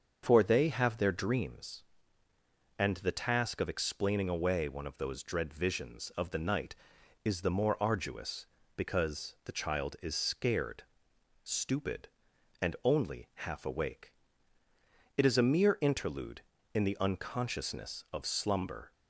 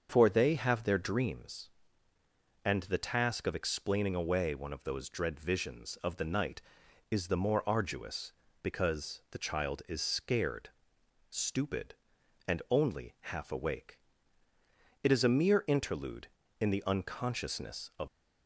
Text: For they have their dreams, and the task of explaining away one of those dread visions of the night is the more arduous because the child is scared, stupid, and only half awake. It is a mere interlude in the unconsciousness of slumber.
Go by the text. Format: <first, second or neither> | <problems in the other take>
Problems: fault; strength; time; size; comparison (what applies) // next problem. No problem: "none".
first | starts louder than the rest; until 1.1 s; 6.5 dB; also in the first // stops before "slumber"; at 18.0 s